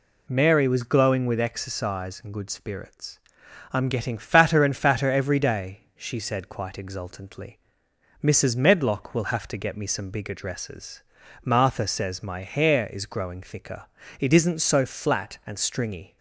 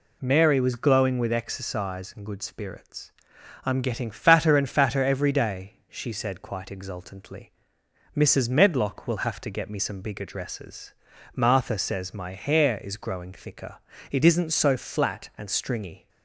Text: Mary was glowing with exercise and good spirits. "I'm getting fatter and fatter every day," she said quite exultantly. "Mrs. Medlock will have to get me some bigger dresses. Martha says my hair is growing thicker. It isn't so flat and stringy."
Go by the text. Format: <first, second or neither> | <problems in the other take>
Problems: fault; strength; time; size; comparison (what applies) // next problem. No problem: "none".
neither | none